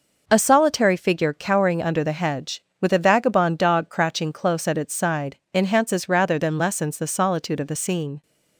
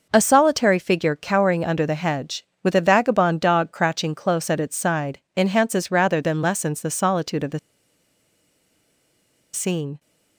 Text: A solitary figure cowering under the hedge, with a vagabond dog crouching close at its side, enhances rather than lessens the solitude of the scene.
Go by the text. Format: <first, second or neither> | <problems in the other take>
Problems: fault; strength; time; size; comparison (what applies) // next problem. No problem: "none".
first | pauses between "the" and "scene"; strong; at 7.5 s; 1.9 s long